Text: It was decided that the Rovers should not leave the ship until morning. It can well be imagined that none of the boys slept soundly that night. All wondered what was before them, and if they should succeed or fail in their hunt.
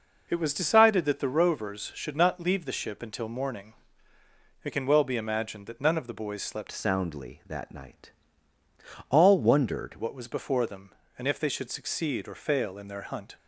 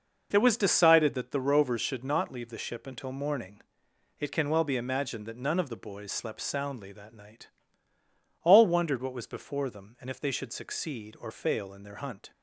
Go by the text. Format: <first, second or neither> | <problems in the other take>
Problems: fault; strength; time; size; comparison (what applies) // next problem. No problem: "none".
second | changes voice from "soundly" to "wondered"; from 6.7 to 9.9 s; 3.2 s long